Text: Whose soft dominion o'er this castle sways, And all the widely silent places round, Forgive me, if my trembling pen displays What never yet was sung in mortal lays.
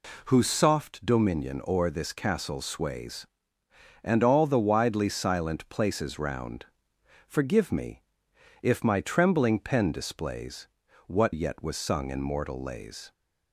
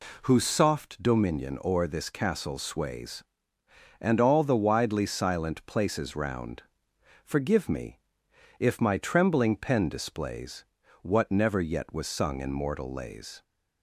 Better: second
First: pauses between "displays" and "What"; at 10.6 s; 0.40 s long // skips "never"; at 11.3 s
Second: pauses between "displays" and "What"; at 10.6 s; 0.38 s long

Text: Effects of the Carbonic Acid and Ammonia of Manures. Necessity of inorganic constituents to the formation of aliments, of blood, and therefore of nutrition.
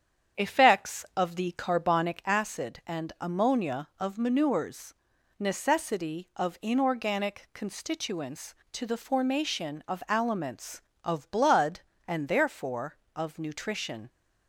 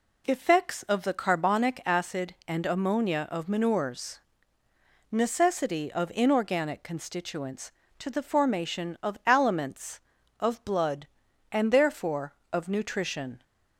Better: second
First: starts louder than the rest; strong; until 2.3 s; 8 dB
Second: none

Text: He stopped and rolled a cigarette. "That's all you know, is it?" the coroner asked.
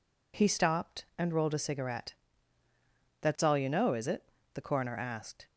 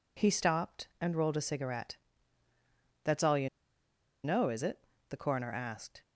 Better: first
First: none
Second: pauses between "you" and "know"; noticeable; at 3.4 s; 0.76 s long

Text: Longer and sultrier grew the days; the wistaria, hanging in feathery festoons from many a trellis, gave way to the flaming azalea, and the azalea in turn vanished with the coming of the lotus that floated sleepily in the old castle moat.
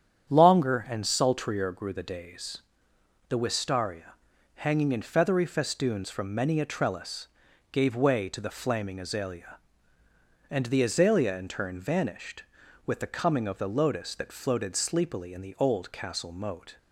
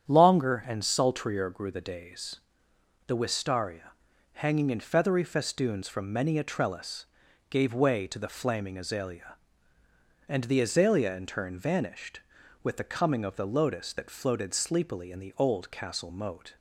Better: neither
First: starts louder than the rest; strong; until 1.3 s; 9 dB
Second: starts louder than the rest; strong; until 1.1 s; 9 dB

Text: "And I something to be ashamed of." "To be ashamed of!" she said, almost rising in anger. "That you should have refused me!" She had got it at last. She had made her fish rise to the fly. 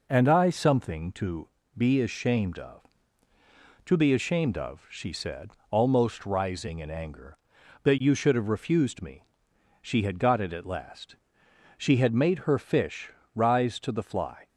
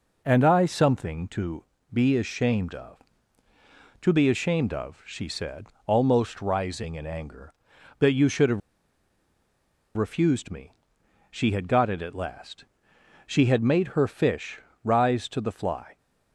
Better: first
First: pauses between "to" and "be"; slight; at 1.4 s; 0.28 s long // pauses between "fish" and "rise"; slight; at 13.1 s; 0.24 s long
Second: pauses between "to" and "be"; slight; at 1.6 s; 0.28 s long // pauses between "have" and "refused"; strong; at 8.6 s; 1.3 s long // pauses between "fish" and "rise"; slight; at 14.6 s; 0.24 s long

